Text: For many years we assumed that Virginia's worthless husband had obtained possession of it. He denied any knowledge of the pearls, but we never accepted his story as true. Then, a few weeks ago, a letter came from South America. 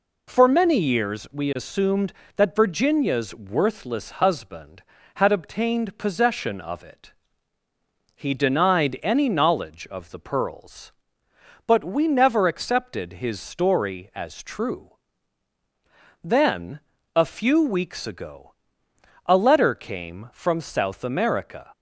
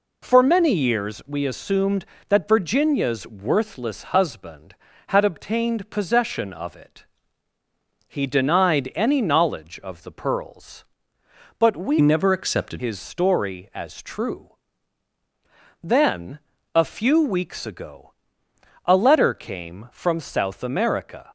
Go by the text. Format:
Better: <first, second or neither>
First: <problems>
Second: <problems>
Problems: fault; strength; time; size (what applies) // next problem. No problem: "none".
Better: first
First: none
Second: changes voice from "never" to "accepted"; from 12.0 to 12.8 s; 0.8 s long